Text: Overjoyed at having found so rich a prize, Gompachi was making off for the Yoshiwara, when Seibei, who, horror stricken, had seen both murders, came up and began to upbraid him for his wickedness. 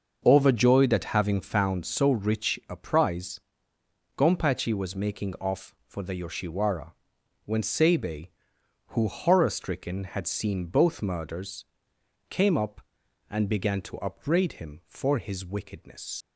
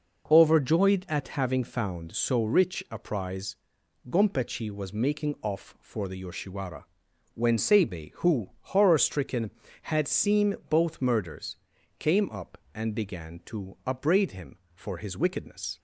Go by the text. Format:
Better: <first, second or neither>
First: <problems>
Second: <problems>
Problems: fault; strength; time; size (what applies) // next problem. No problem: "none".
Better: second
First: starts louder than the rest; until 1.2 s; 6 dB // leaves "wickedness" unfinished; at 16.2 s; 110 ms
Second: none